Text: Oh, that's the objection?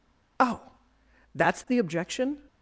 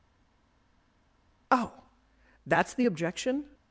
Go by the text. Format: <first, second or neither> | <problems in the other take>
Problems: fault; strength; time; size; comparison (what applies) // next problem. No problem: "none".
first | stays silent before the first word; noticeable; until 1.4 s; 1.4 s long